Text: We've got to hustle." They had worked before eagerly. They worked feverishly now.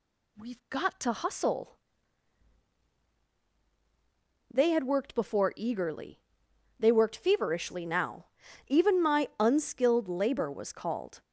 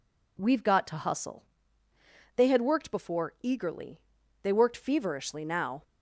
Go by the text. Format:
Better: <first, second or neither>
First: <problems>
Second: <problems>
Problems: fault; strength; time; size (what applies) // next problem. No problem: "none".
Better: second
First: goes on to say "Even my unskilled labor was called"; strong; from 8.6 s on; 2.5 s long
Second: none